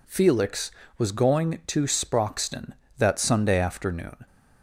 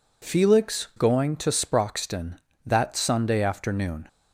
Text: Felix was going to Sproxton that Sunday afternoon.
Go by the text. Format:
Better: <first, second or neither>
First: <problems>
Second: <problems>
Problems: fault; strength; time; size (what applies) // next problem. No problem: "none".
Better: first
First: none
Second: skips "was"; at 0.9 s